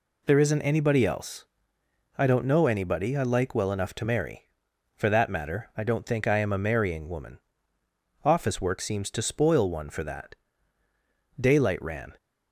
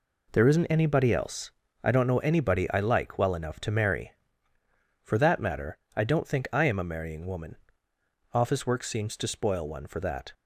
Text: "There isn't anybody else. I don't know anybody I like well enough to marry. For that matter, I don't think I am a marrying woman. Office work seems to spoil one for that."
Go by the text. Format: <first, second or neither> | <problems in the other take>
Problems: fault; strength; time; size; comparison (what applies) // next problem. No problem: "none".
second | goes on to say "Daylight ran"; noticeable; from 11.3 s on; 0.74 s long